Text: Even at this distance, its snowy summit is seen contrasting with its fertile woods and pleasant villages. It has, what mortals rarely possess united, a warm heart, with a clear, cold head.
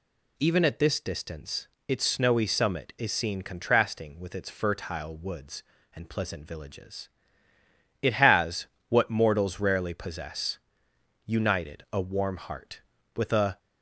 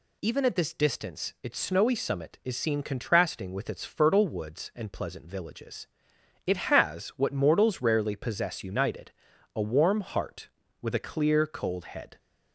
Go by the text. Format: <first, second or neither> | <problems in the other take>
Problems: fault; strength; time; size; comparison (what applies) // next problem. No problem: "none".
second | pauses between "possess" and "united"; noticeable; at 10.5 s; 0.70 s long // stops before "clear cold head"; at 13.5 s